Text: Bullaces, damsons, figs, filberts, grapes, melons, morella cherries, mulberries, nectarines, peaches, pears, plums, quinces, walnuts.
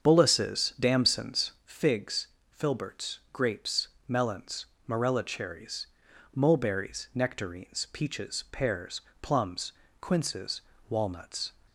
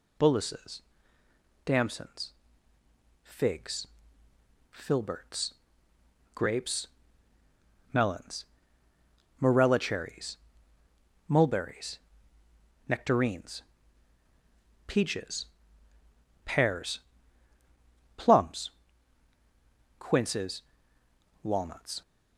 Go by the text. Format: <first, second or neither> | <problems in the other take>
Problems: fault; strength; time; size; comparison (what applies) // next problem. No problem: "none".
second | starts louder than the rest; strong; until 1.8 s; 7.5 dB